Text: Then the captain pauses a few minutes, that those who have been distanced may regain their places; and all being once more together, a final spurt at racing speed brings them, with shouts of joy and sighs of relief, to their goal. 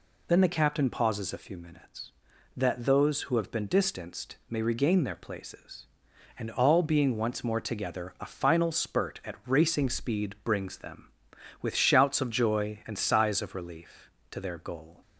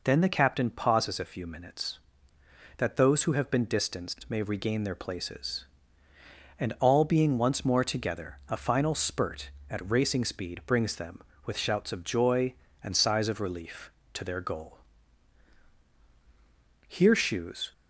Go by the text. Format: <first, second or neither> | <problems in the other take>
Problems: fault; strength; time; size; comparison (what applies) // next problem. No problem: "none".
first | goes on to say "Here shoes"; noticeable; from 16.8 s on; 0.84 s long